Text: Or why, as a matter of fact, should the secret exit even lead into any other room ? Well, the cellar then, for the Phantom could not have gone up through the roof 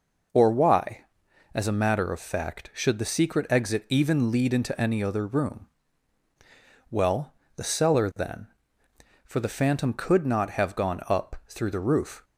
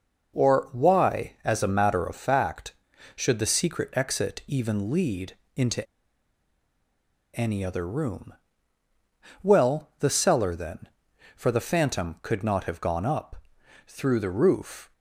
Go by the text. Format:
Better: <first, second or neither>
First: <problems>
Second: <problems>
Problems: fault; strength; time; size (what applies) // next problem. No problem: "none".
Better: first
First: none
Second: pauses between "lead" and "into"; slight; at 5.3 s; 0.18 s long // pauses between "into" and "any"; strong; at 5.8 s; 1.5 s long // pauses between "up" and "through"; noticeable; at 13.3 s; 0.50 s long